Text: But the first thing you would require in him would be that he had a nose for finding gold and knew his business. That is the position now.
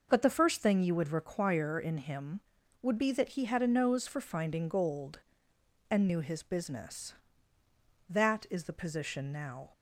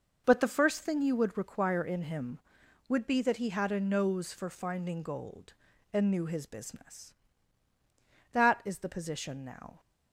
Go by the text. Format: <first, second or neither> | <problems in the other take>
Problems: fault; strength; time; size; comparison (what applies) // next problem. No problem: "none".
neither | none